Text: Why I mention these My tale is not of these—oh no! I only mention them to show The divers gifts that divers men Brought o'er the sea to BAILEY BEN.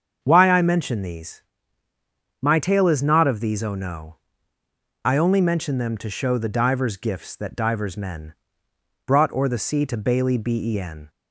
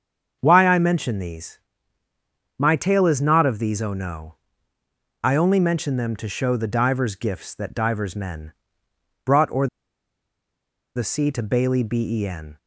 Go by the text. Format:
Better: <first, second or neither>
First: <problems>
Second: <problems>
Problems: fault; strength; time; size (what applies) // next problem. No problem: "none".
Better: first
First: starts louder than the rest; until 1.2 s; 7 dB // pauses between "these" and "My"; at 1.4 s; 1.0 s long // pauses between "men" and "Brought"; noticeable; at 8.3 s; 0.72 s long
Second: starts louder than the rest; until 1.4 s; 7 dB // pauses between "these" and "My"; at 1.5 s; 1.0 s long // pauses between "men" and "Brought"; noticeable; at 8.5 s; 0.72 s long // pauses between "o'er" and "the"; strong; at 9.6 s; 1.2 s long